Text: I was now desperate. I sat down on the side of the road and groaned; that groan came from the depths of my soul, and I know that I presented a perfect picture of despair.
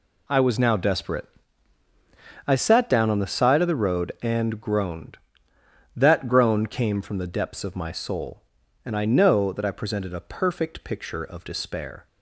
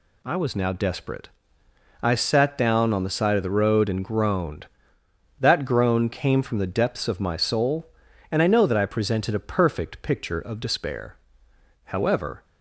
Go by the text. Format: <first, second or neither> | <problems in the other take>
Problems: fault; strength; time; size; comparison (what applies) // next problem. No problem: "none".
first | goes on to say "However"; from 11.8 s on; 0.58 s long